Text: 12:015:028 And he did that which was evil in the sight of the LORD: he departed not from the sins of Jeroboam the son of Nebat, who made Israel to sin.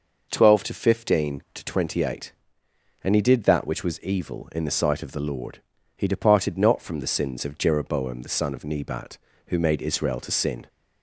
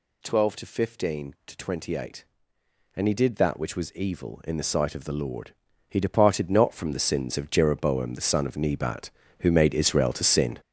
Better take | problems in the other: first | gets louder; strong; throughout; 8 dB

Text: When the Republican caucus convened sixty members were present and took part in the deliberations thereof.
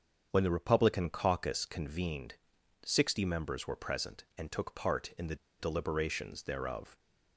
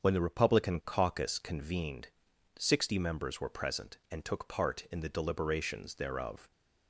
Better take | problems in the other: second | starts louder than the rest; until 1.3 s; 7 dB; also in the second // pauses between "convened" and "sixty"; noticeable; at 2.3 s; 0.50 s long; noticeable in the second // pauses between "the" and "deliberations"; slight; at 5.3 s; 0.24 s long

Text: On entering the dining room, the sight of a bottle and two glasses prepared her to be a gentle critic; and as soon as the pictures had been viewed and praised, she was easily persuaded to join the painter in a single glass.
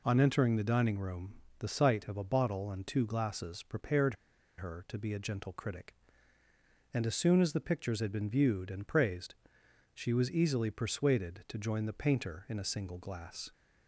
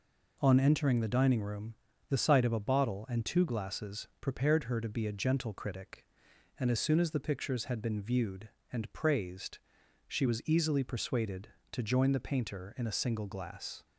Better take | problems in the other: second | pauses between "prepared" and "her"; at 4.1 s; 0.44 s long

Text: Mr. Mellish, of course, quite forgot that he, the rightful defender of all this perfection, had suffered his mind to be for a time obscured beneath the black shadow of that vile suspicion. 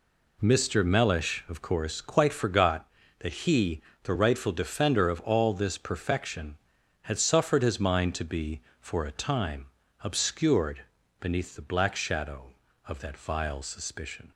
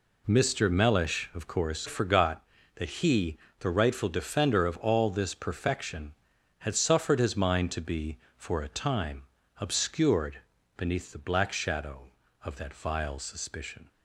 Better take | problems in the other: first | skips "quite"; at 1.8 s // pauses between "time" and "obscured"; slight; at 9.2 s; 0.36 s long; slight in the first // pauses between "obscured" and "beneath"; slight; at 10.3 s; 0.36 s long; slight in the first

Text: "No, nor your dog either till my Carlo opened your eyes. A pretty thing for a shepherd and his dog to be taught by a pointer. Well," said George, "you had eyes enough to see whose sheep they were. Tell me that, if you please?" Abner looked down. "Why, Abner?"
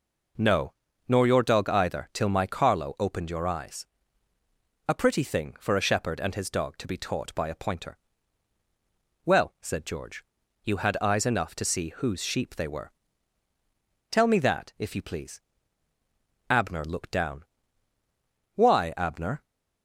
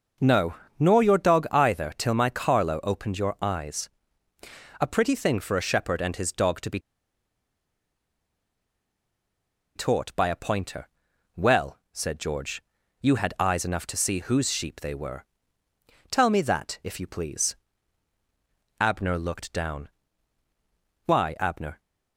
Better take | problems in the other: first | pauses between "be" and "taught"; strong; at 6.7 s; 2.9 s long

